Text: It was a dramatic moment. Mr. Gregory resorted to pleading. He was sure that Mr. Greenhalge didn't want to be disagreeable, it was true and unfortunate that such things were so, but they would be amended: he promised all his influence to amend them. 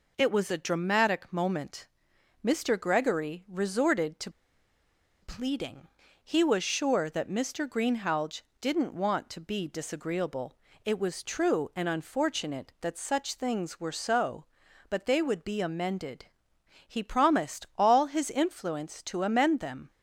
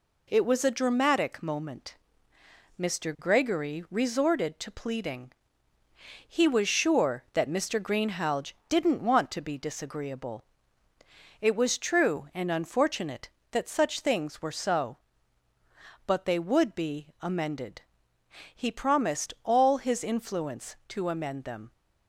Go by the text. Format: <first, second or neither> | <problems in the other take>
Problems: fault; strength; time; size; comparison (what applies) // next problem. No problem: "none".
second | pauses between "to" and "pleading"; noticeable; at 4.3 s; 0.91 s long // pauses between "Greenhalge" and "didn't"; slight; at 8.3 s; 0.22 s long; slight in the second